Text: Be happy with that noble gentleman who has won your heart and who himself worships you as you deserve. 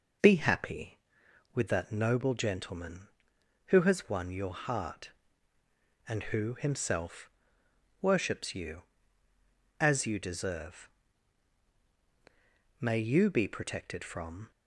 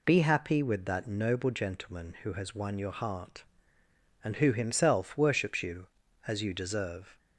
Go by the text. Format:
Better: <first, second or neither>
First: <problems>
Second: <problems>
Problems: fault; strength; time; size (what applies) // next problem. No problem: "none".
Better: second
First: pauses between "himself" and "worships"; noticeable; at 7.3 s; 0.72 s long // goes on to say "May you be protected from"; strong; from 12.7 s on; 1.7 s long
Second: none